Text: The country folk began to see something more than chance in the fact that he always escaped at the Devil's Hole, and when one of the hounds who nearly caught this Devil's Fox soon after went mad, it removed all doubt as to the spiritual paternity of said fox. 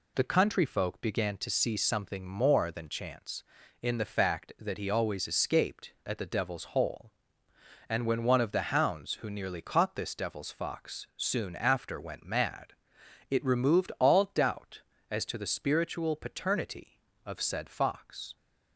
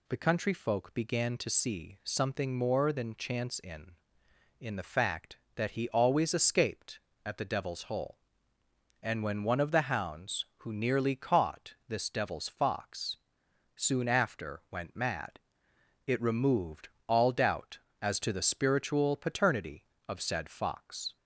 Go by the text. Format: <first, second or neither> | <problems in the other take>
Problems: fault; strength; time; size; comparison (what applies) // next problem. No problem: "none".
first | says "in" twice; at 4.5 s // pauses between "Fox" and "soon"; noticeable; at 13.1 s; 0.58 s long // pauses between "removed" and "all"; slight; at 16.8 s; 0.20 s long